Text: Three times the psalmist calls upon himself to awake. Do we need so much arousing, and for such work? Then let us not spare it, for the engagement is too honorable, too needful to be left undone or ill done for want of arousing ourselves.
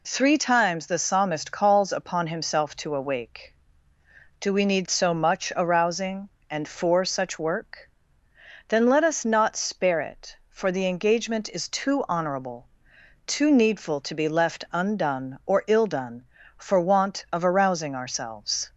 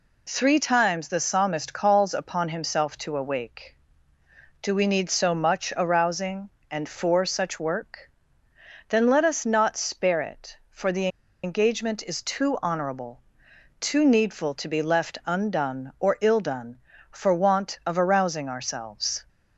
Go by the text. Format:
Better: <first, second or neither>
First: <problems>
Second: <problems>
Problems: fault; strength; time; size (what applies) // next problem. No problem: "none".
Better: first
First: none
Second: pauses between "the" and "engagement"; slight; at 11.0 s; 0.35 s long